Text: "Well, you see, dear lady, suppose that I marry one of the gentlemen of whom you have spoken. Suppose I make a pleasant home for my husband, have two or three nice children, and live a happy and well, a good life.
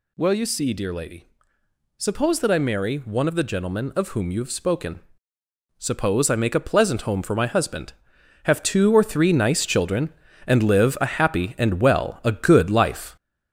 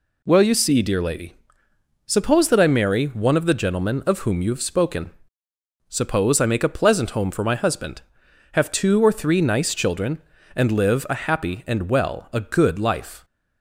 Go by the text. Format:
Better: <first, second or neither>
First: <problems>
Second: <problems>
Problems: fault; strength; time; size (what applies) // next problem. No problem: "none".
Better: second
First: gets louder; noticeable; throughout; 5 dB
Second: none